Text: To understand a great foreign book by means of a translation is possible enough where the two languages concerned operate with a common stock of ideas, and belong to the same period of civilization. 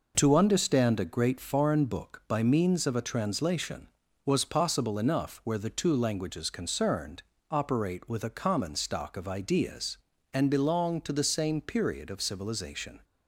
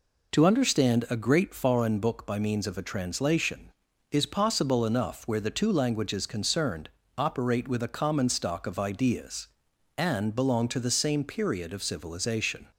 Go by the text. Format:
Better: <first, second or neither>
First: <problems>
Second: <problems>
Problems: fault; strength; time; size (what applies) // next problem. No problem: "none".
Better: second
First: says "was" for "is"; at 4.2 s // pauses between "concerned" and "operate"; slight; at 7.2 s; 0.28 s long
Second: pauses between "concerned" and "operate"; slight; at 6.8 s; 0.27 s long